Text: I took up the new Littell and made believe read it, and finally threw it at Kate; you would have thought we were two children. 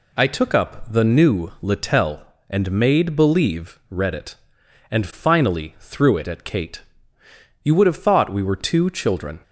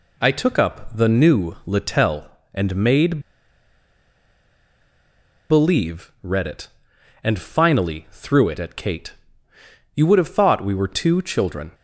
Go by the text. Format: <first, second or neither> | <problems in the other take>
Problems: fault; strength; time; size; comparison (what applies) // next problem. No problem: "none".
first | pauses between "made" and "believe"; strong; at 3.2 s; 2.2 s long